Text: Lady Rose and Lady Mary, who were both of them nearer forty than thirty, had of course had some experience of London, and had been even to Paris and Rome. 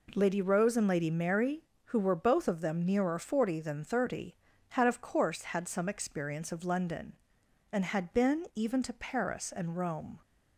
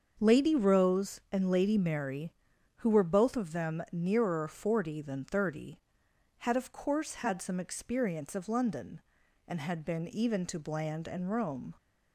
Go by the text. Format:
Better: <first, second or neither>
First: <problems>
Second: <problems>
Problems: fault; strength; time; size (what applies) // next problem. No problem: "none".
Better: first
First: none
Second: starts louder than the rest; until 1.2 s; 7 dB // says "Bland" for "Paris"; at 10.5 s